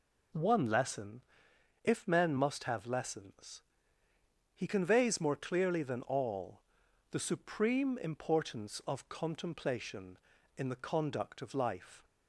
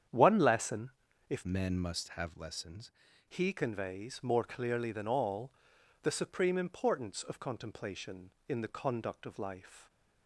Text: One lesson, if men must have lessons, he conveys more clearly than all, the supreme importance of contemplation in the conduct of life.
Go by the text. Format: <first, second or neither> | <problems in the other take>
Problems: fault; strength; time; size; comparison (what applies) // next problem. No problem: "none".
first | starts louder than the rest; strong; until 1.4 s; 8.5 dB // changes voice from "men" to "lessons"; from 1.4 to 2.9 s; 1.5 s long